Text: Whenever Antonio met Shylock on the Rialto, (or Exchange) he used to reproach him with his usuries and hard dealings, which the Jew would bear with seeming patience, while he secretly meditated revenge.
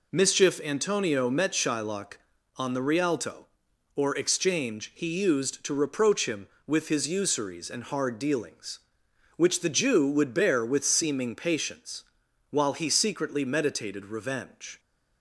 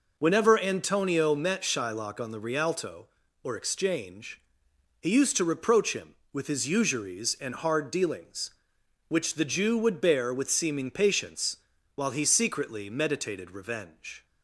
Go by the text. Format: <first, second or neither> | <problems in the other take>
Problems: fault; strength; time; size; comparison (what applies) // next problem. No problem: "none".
second | says "Mischief" for "Whenever"; at 0.1 s